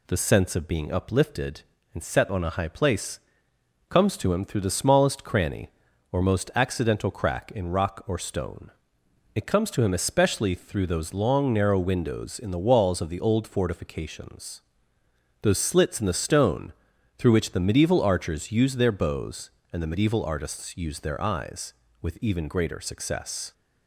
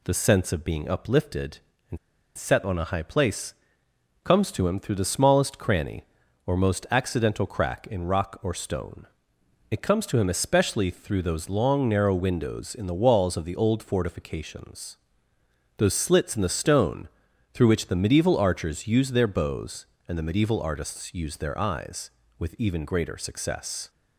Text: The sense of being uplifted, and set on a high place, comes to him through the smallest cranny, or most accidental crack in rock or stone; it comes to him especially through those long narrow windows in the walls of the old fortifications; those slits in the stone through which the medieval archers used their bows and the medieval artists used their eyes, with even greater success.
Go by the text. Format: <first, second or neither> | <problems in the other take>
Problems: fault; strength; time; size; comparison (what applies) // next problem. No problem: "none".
first | pauses between "and" and "set"; at 1.9 s; 0.39 s long // pauses between "stone" and "through"; at 17.0 s; 0.42 s long; also in the first